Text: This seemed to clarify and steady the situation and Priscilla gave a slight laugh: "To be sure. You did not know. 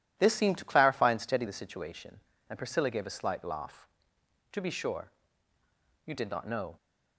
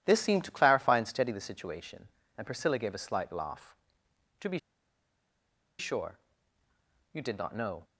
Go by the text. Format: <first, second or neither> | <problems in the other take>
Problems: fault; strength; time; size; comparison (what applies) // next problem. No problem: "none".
first | pauses between "be" and "sure"; at 4.5 s; 1.2 s long